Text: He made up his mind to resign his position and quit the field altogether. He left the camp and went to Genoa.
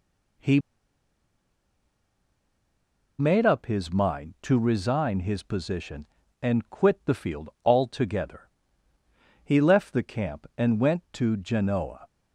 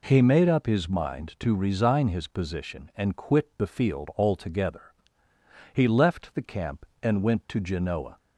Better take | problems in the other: second | pauses between "He" and "made"; strong; at 0.6 s; 2.5 s long

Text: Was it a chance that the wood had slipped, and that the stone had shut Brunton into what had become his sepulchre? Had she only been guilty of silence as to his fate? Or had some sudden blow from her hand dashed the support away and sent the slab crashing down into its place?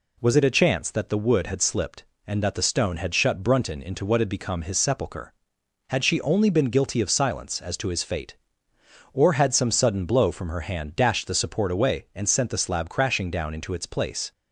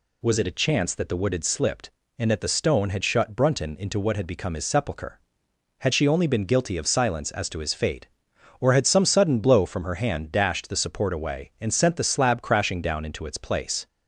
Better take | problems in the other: neither | none

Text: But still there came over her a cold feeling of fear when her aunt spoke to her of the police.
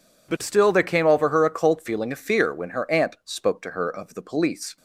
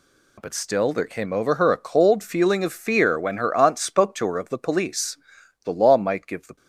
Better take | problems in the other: first | goes on to say "The law might give the"; noticeable; from 5.6 s on; 0.92 s long

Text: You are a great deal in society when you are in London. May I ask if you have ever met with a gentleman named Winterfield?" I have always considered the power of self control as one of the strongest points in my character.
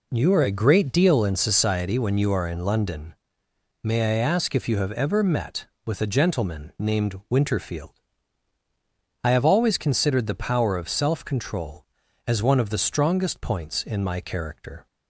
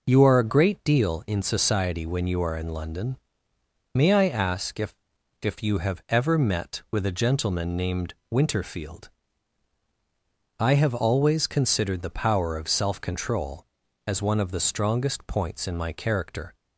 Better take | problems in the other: first | says "if" twice; at 5.3 s // pauses between "named" and "Winterfield"; slight; at 8.1 s; 0.18 s long

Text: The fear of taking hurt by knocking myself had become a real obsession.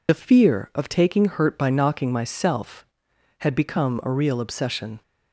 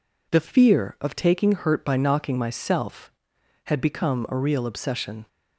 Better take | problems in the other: second | loses the start of "The"; at 0.0 s; 45 ms

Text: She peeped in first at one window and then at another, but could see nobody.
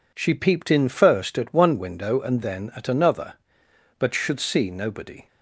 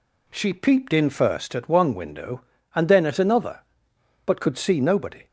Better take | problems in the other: second | says "should" for "could"; at 4.1 s

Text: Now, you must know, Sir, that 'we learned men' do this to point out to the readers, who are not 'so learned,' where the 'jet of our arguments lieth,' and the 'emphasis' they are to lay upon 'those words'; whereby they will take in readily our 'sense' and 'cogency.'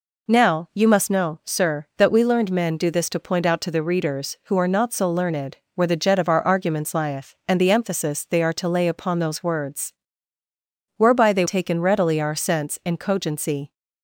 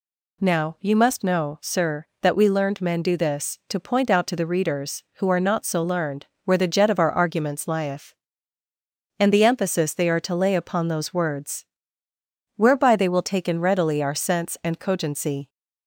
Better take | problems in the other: second | skips "will"; at 11.4 s

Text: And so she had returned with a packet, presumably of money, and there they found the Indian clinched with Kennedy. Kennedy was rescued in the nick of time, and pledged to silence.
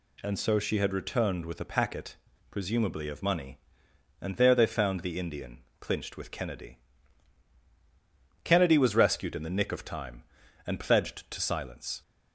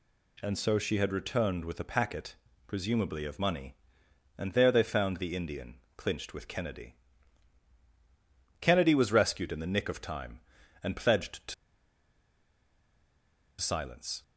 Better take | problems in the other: first | pauses between "Indian" and "clinched"; slight; at 5.7 s; 0.20 s long; slight in the first // pauses between "to" and "silence"; strong; at 11.5 s; 2.0 s long

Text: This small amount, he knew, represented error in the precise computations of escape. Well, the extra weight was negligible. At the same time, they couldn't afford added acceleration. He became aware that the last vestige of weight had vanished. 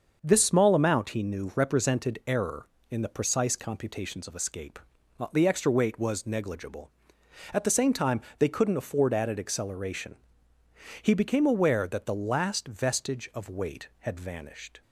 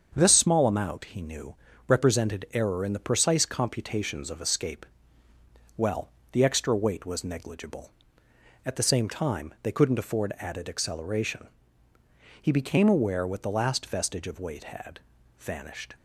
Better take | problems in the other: first | starts louder than the rest; until 1.1 s; 7 dB; also in the first // says "what" for "that"; at 13.2 s // pauses between "had" and "vanished"; at 14.9 s; 0.40 s long

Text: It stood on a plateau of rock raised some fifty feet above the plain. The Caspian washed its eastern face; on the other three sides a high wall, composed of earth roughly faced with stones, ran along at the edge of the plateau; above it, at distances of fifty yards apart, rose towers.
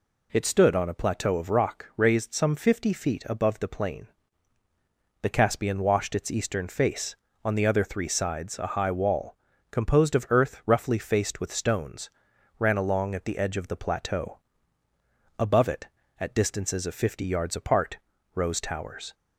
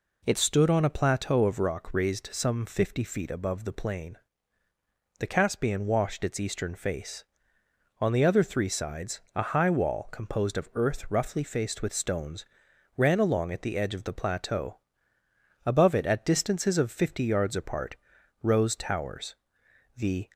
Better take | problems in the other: first | pauses between "sides" and "a"; slight; at 9.1 s; 0.16 s long // goes on to say "The"; slight; from 19.9 s on; 0.32 s long

